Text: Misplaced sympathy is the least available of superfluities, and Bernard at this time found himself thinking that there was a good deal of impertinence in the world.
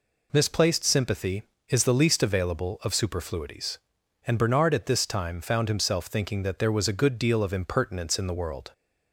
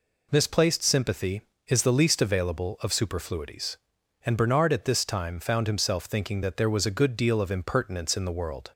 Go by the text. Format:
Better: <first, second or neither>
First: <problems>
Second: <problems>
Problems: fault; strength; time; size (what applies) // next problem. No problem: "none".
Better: neither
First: none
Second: none